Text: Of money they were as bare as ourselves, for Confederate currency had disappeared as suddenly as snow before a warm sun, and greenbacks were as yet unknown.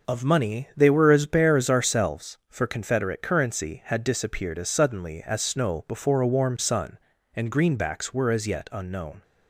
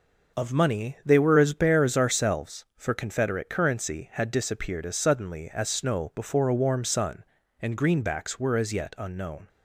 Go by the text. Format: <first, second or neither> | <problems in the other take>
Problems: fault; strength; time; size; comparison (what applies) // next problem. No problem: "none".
neither | none